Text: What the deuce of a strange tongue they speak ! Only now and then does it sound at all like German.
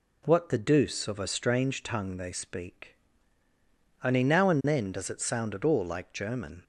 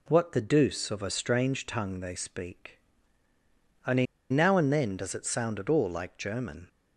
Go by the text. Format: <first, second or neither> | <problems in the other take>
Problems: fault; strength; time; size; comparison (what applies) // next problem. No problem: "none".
first | pauses between "Only" and "now"; slight; at 4.0 s; 0.26 s long